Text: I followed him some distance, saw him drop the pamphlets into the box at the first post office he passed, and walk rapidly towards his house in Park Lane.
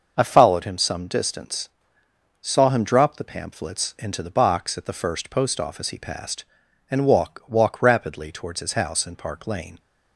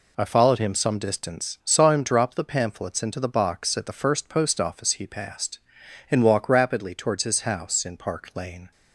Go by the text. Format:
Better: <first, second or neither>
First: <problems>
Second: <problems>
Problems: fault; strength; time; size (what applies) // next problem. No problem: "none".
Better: second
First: starts louder than the rest; noticeable; until 1.1 s; 6 dB // says "walk" twice; at 7.4 s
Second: none